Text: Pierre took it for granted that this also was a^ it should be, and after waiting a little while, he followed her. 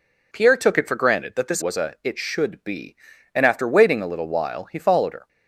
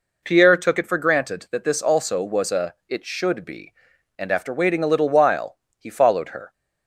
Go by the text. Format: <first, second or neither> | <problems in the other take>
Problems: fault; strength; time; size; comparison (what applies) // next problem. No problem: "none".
second | skips "also"; at 1.6 s